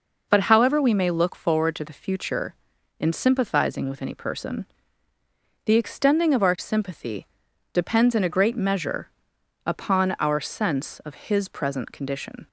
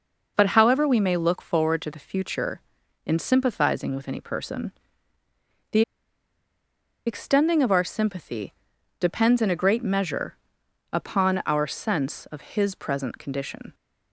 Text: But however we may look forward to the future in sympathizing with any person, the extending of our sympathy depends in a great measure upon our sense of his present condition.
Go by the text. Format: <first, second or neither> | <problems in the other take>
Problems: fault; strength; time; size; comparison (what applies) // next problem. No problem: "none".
first | pauses between "the" and "extending"; strong; at 5.8 s; 1.2 s long // pauses between "sympathy" and "depends"; noticeable; at 8.5 s; 0.48 s long; noticeable in the first // pauses between "measure" and "upon"; noticeable; at 10.3 s; 0.56 s long; noticeable in the first